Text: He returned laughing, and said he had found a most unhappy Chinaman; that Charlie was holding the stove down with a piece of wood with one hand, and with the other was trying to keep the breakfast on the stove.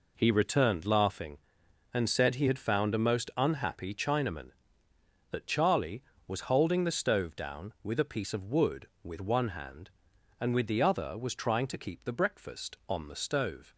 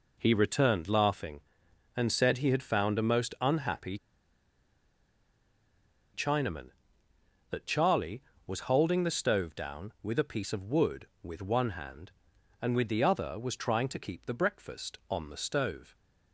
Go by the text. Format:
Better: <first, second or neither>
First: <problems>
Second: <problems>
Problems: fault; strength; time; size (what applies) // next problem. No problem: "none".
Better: first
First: none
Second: pauses between "unhappy" and "Chinaman"; strong; at 3.9 s; 2.1 s long